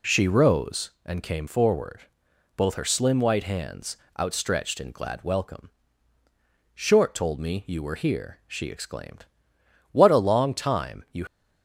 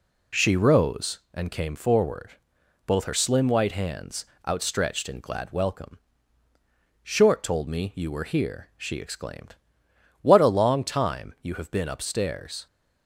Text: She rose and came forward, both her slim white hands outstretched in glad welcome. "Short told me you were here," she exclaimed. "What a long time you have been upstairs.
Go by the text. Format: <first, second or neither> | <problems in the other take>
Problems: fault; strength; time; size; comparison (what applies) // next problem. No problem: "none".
second | pauses between "hands" and "outstretched"; slight; at 3.9 s; 0.24 s long; slight in the second // stops before "have been upstairs"; at 11.2 s